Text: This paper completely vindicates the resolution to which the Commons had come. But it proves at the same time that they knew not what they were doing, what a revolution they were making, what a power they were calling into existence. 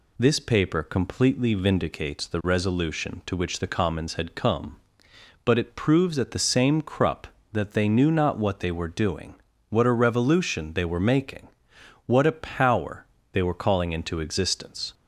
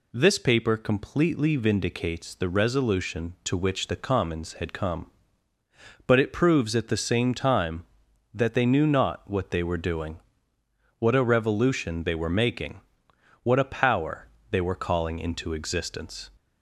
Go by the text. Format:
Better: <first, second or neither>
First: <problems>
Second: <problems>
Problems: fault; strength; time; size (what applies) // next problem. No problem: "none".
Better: second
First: says "crup" for "time"; at 6.8 s // pauses between "power" and "they"; slight; at 13.0 s; 0.26 s long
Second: pauses between "power" and "they"; slight; at 14.2 s; 0.24 s long